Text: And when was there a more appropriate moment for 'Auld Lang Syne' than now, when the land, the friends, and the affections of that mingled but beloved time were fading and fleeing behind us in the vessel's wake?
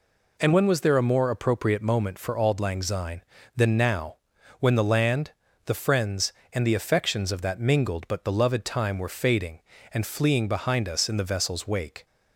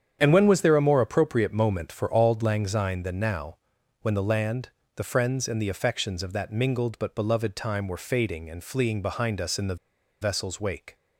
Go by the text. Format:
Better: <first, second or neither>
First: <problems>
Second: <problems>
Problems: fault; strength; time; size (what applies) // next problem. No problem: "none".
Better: first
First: none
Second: starts louder than the rest; strong; until 1.2 s; 8.5 dB // pauses between "the" and "vessel's"; at 9.7 s; 0.45 s long